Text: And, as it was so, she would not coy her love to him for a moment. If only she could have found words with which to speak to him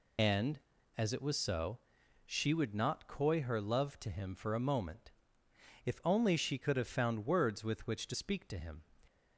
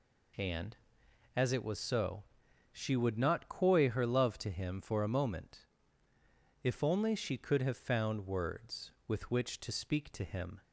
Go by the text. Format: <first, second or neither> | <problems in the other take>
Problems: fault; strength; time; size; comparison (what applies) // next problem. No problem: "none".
second | loses the start of "And"; at 0.1 s; 65 ms